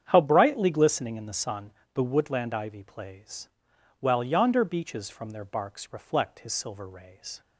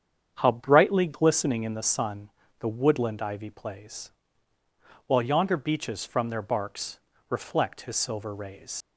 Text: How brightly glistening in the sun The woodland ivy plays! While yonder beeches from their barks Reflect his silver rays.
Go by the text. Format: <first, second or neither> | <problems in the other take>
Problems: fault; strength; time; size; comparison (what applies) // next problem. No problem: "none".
first | starts louder than the rest; strong; until 1.3 s; 8 dB; strong in the first // pauses between "sun" and "The"; slight; at 2.3 s; 0.28 s long; slight in the first // pauses between "barks" and "Reflect"; slight; at 6.9 s; 0.30 s long // leaves "rays" unfinished; at 8.8 s; 85 ms